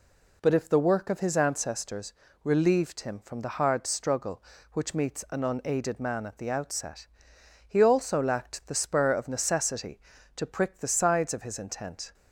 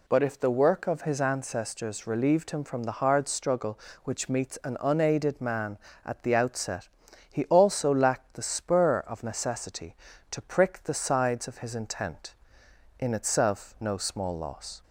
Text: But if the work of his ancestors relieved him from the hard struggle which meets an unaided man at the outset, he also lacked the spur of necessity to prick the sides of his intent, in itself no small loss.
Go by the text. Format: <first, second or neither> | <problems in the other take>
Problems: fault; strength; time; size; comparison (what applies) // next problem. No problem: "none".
second | pauses between "ancestors" and "relieved"; slight; at 2.1 s; 0.30 s long // stops before "in itself no small loss"; at 12.1 s